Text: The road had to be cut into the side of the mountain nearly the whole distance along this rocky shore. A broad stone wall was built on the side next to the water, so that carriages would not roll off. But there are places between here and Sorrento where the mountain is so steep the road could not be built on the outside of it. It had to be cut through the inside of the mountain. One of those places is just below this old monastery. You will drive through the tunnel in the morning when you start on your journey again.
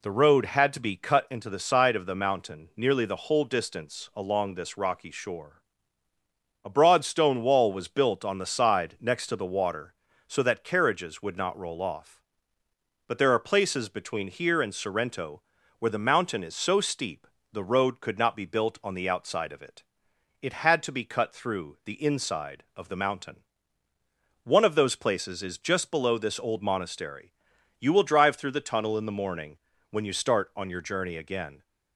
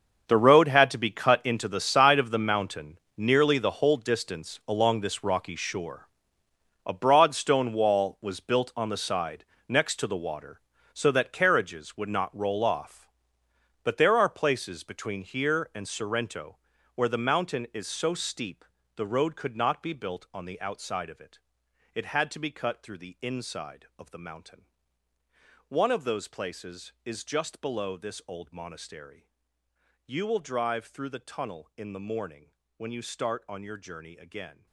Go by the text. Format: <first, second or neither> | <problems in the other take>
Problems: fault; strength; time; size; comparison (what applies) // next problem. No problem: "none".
first | gets quieter; strong; throughout; 14.5 dB // pauses between "mountain" and "nearly"; slight; at 2.9 s; 0.18 s long // pauses between "side" and "next"; slight; at 9.4 s; 0.24 s long // pauses between "Sorrento" and "where"; at 16.5 s; 0.38 s long; also in the first // pauses between "steep" and "the"; slight; at 18.6 s; 0.32 s long; slight in the first // pauses between "morning" and "when"; slight; at 32.5 s; 0.26 s long; slight in the first